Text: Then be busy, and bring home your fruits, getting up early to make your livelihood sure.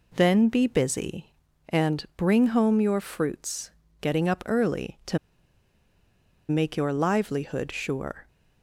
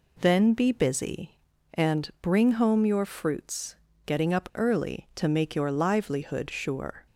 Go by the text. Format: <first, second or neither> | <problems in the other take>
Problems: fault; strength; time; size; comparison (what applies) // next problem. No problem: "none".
second | pauses between "to" and "make"; strong; at 5.1 s; 1.3 s long